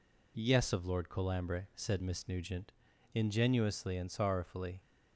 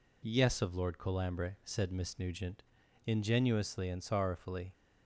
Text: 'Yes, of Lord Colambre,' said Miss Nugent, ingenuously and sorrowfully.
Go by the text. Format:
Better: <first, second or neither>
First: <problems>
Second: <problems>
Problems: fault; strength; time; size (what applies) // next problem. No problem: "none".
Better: neither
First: none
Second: none